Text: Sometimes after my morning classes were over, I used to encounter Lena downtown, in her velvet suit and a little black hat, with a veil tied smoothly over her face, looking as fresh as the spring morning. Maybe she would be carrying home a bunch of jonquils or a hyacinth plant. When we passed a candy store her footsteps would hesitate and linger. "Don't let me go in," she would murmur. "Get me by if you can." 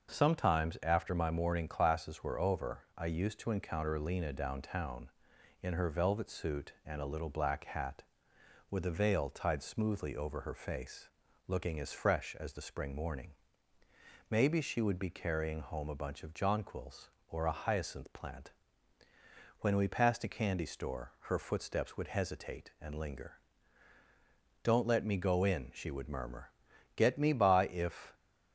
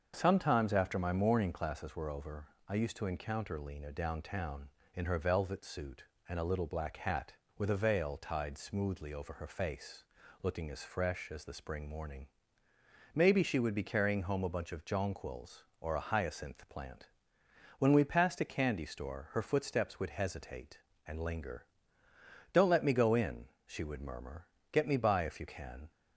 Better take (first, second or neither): second